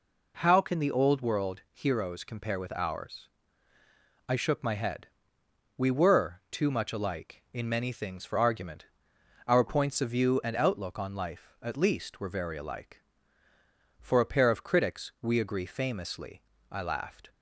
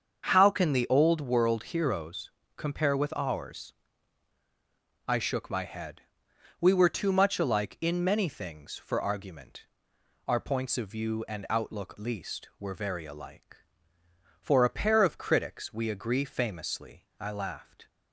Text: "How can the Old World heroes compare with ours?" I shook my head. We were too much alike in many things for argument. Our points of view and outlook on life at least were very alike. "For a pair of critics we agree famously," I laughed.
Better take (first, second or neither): first